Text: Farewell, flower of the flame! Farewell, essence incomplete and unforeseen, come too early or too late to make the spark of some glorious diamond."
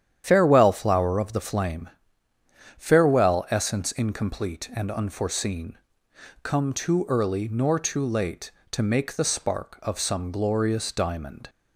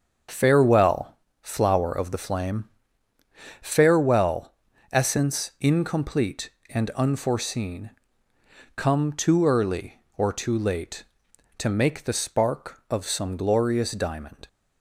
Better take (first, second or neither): second